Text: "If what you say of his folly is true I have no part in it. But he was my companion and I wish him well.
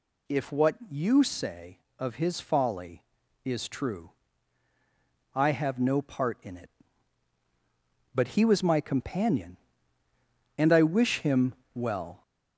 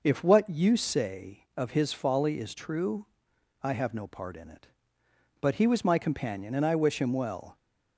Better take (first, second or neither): second